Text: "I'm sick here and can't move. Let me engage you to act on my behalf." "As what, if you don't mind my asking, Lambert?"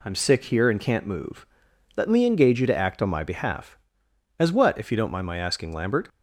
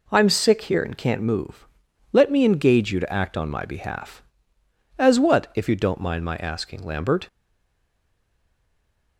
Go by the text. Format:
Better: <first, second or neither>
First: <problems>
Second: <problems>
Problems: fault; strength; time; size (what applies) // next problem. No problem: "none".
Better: first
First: none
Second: stays silent after the last word; noticeable; from 7.2 s on; 1.9 s long